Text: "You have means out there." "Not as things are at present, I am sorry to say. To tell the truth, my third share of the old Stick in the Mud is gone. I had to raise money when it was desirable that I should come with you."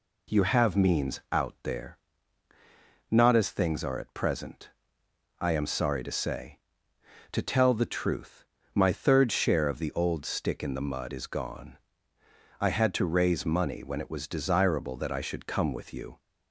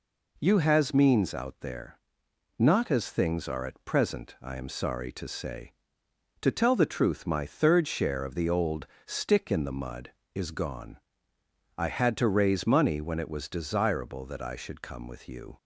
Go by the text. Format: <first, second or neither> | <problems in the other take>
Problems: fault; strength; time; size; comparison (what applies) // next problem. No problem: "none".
first | says "has" for "have"; at 0.5 s // pauses between "old" and "Stick"; slight; at 8.8 s; 0.22 s long